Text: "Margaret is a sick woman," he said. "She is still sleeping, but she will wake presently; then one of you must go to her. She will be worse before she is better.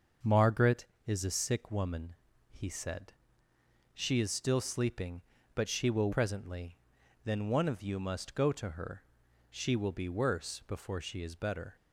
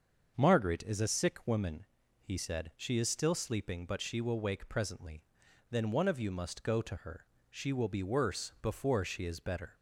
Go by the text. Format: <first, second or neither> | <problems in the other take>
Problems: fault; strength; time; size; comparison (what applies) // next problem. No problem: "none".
second | starts louder than the rest; until 1.4 s; 6.5 dB; also in the second // skips "wake"; at 6.1 s